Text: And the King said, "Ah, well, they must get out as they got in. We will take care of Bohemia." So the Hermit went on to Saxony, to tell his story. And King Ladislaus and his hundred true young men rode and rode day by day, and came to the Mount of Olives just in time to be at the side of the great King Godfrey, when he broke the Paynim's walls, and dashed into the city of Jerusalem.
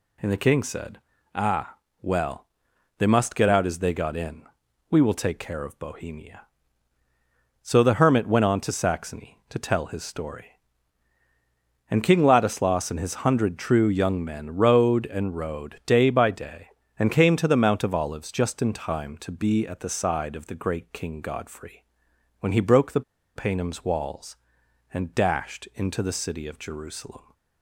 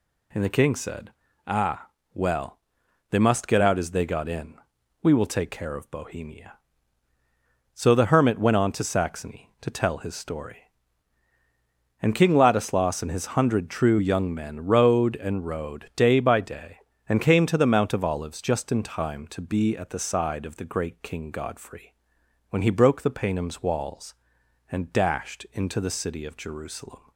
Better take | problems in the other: second | pauses between "the" and "Paynim's"; slight; at 23.0 s; 0.34 s long

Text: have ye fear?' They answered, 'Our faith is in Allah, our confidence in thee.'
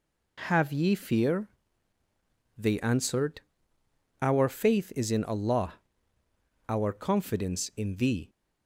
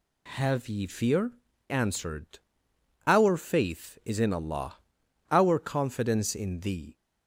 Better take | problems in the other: first | skips "They"; at 1.5 s

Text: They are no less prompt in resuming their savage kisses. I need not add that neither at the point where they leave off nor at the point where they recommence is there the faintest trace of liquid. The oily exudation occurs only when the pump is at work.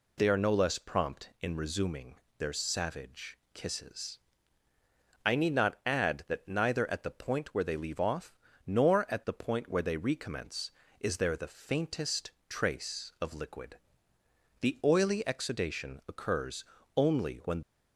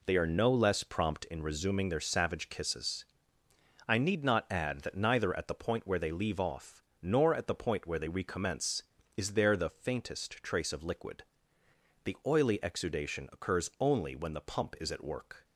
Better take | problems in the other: second | pauses between "resuming" and "their"; slight; at 2.1 s; 0.24 s long // pauses between "off" and "nor"; slight; at 8.3 s; 0.34 s long; slight in the second // pauses between "faintest" and "trace"; slight; at 12.3 s; 0.16 s long // pauses between "occurs" and "only"; slight; at 16.6 s; 0.30 s long // stops before "the pump is at work"; at 17.6 s

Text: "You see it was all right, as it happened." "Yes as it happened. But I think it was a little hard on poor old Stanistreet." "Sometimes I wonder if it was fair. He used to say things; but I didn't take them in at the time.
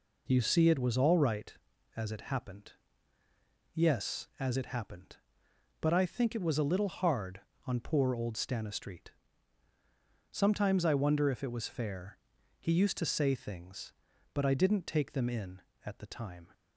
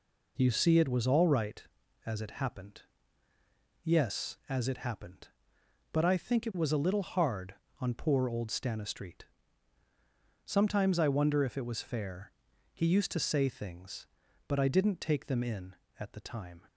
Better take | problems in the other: neither | none

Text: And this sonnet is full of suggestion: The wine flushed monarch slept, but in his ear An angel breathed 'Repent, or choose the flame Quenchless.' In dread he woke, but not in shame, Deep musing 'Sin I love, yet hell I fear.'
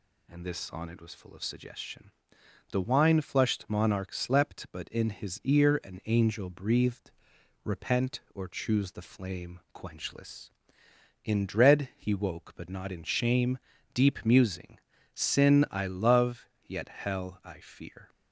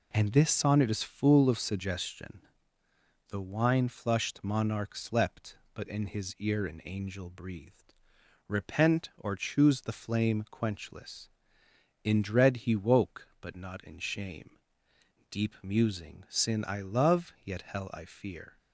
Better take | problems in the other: second | says "was" for "is"; at 1.0 s // pauses between "breathed" and "Repent"; noticeable; at 7.1 s; 0.54 s long; noticeable in the second // pauses between "musing" and "Sin"; slight; at 14.7 s; 0.34 s long

